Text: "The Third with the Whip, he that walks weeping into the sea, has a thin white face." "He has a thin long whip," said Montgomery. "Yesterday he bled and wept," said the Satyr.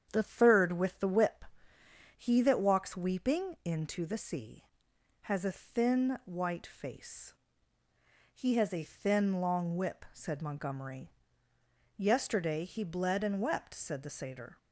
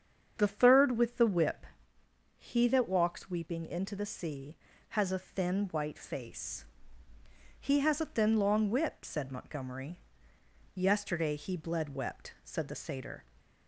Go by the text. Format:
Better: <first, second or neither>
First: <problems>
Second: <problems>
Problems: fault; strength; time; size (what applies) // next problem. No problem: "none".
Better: first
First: starts louder than the rest; strong; until 1.1 s; 8 dB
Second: starts louder than the rest; strong; until 1.3 s; 7.5 dB // skips "and"; at 11.9 s